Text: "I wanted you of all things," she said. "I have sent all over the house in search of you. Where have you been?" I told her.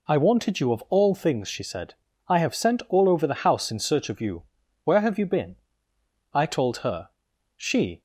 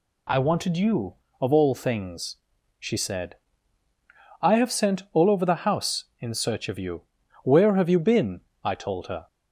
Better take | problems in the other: second | goes on to say "She"; slight; from 7.5 s on; 0.46 s long

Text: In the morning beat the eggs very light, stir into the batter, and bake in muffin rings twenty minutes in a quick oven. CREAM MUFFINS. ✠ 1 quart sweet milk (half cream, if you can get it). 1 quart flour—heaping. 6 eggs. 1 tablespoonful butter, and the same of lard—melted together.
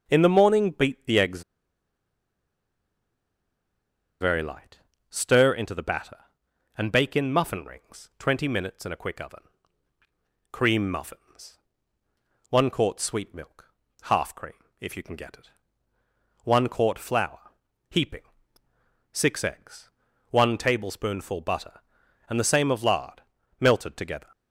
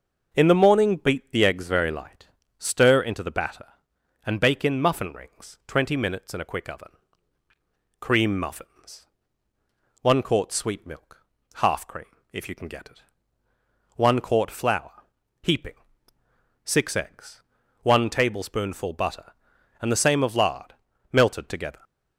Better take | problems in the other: second | pauses between "eggs" and "very"; strong; at 1.4 s; 2.7 s long

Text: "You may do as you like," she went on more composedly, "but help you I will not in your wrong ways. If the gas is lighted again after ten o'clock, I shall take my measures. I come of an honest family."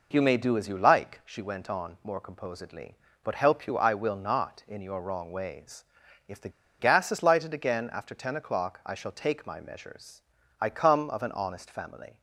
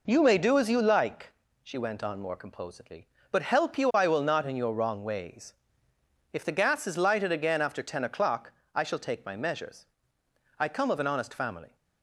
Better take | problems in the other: second | pauses between "the" and "gas"; slight; at 6.4 s; 0.29 s long

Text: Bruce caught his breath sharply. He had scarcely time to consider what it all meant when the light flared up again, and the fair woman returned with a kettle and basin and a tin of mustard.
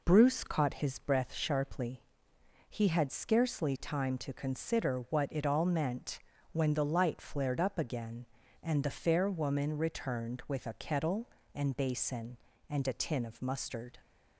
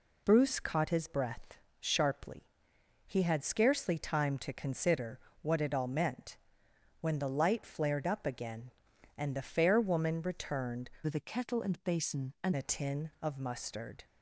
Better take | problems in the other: first | pauses between "breath" and "sharply"; slight; at 1.5 s; 0.20 s long // pauses between "consider" and "what"; slight; at 5.1 s; 0.22 s long // pauses between "meant" and "when"; noticeable; at 6.3 s; 0.64 s long; slight in the first // changes voice from "with" to "and"; from 11.0 to 12.5 s; 1.5 s long

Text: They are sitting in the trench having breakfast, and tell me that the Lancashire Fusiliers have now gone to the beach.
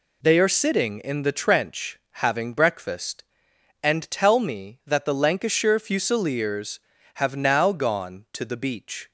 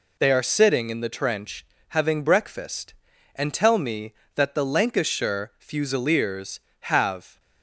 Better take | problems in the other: first | pauses between "trench" and "having"; slight; at 1.6 s; 0.24 s long; slight in the first // stops before "now gone to the beach"; at 7.3 s

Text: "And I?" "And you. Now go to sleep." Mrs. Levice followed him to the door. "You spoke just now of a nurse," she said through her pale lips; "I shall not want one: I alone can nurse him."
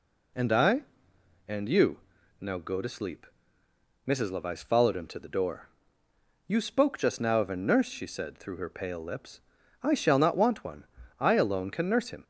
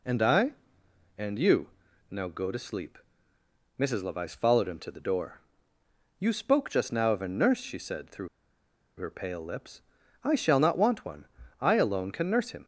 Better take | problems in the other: first | pauses between "through" and "her"; noticeable; at 8.2 s; 0.69 s long

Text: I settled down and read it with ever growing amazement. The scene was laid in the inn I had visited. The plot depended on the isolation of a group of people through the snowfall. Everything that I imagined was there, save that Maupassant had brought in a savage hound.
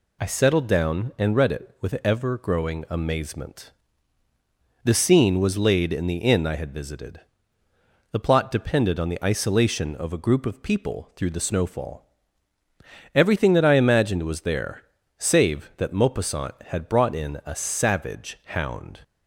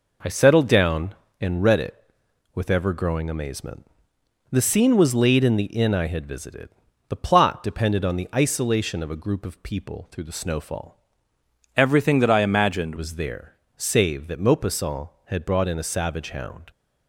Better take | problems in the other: first | changes voice from "Everything" to "imagined"; from 11.7 to 12.9 s; 1.2 s long

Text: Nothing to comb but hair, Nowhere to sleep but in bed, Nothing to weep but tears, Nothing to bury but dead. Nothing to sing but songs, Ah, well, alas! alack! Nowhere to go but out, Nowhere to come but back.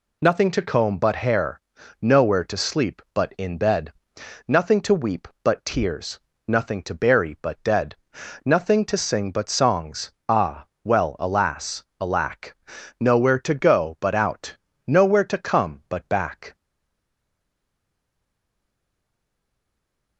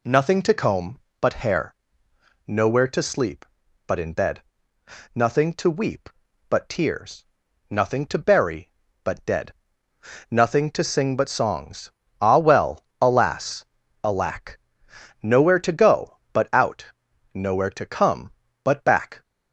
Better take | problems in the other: second | stays silent after the last word; strong; from 16.5 s on; 3.6 s long

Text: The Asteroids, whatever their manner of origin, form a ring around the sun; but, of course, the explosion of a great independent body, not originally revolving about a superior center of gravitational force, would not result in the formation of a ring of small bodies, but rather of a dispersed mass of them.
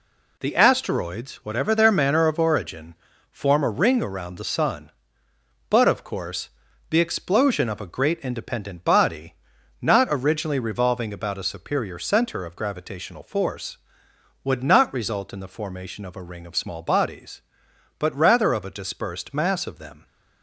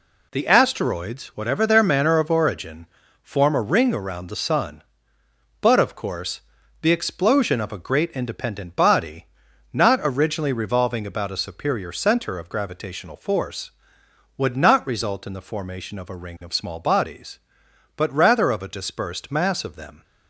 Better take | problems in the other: neither | none

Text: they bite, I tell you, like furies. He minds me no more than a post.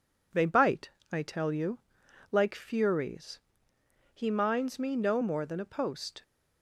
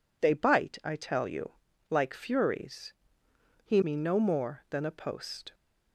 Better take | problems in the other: first | skips "minds"; at 3.8 s

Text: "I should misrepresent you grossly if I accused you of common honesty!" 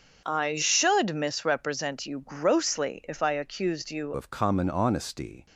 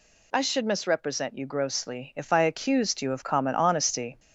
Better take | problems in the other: second | starts louder than the rest; until 1.2 s; 7 dB // changes voice at "of"; from 4.1 s on; 1.3 s long

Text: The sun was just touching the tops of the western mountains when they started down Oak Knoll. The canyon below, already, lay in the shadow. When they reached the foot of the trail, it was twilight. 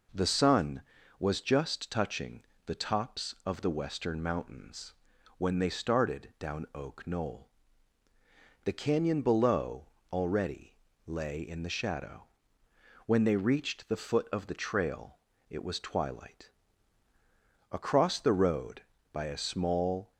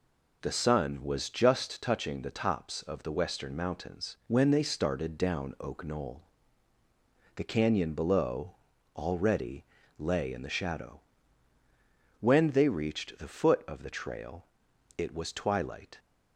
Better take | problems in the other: second | pauses between "touching" and "the"; slight; at 2.4 s; 0.22 s long // pauses between "mountains" and "when"; at 4.9 s; 0.44 s long // goes on to say "Across the road by a small"; strong; from 17.7 s on; 2.4 s long

